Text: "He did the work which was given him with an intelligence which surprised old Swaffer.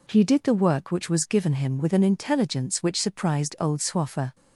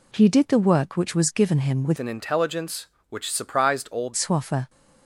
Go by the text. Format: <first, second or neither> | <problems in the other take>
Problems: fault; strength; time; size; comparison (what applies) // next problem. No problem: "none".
first | changes voice from "an" to "old"; from 1.9 to 4.1 s; 2.2 s long